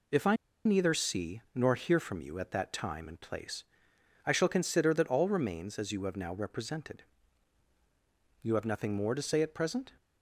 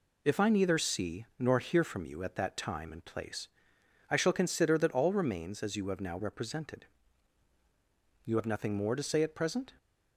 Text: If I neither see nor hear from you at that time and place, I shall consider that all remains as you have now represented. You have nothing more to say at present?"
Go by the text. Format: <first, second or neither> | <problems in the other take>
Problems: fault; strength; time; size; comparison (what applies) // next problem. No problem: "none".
second | pauses between "I" and "neither"; slight; at 0.3 s; 0.30 s long